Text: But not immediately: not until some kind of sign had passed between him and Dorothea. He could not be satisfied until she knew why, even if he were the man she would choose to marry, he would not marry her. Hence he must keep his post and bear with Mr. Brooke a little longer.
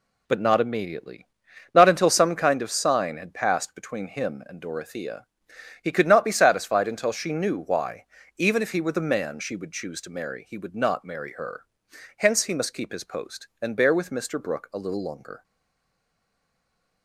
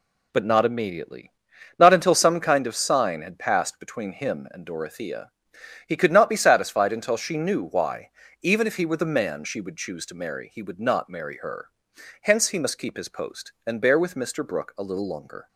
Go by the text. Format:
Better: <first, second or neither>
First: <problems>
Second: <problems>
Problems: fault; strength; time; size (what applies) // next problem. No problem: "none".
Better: second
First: stays silent after the last word; noticeable; from 15.4 s on; 1.6 s long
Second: none